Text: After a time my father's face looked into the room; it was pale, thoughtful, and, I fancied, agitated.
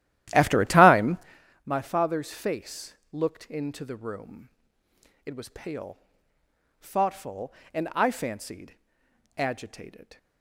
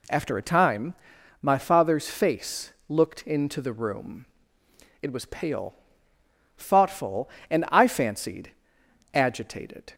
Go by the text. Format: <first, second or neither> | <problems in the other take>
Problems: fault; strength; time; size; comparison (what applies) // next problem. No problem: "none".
second | starts louder than the rest; strong; until 1.4 s; 13 dB // pauses between "time" and "my"; noticeable; at 1.1 s; 0.48 s long; noticeable in the second // pauses between "face" and "looked"; slight; at 2.9 s; 0.18 s long; slight in the second